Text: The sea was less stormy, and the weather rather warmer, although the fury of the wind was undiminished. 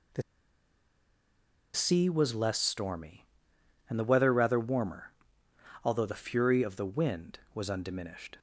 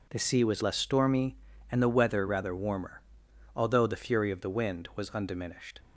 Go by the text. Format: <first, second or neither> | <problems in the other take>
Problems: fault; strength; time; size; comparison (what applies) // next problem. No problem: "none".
second | pauses between "The" and "sea"; strong; at 0.2 s; 1.5 s long